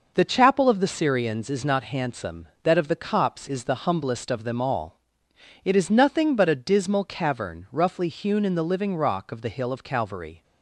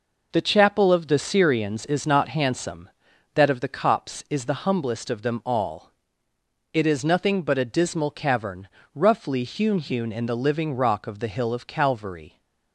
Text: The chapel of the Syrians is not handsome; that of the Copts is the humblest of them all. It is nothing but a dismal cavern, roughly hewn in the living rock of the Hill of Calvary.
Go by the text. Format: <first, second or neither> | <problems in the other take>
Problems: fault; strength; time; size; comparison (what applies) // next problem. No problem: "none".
first | says "hewn" twice; at 9.7 s